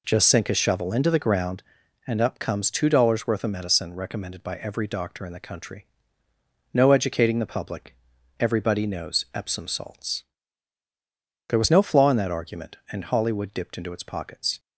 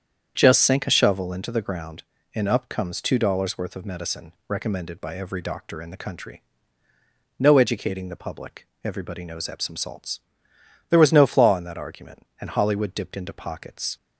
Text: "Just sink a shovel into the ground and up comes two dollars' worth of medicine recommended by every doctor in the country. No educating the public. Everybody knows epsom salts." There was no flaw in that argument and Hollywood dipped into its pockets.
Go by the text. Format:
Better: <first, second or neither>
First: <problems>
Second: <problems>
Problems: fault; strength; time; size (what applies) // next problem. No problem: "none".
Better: first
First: none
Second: starts louder than the rest; strong; until 1.3 s; 8 dB // pauses between "medicine" and "recommended"; slight; at 4.3 s; 0.16 s long // skips "its"; at 13.3 s